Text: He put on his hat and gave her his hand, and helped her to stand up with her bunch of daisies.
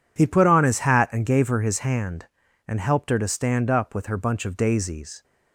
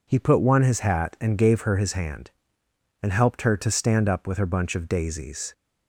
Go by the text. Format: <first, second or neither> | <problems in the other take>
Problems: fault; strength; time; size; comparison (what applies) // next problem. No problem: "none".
first | says "one" for "on"; at 0.4 s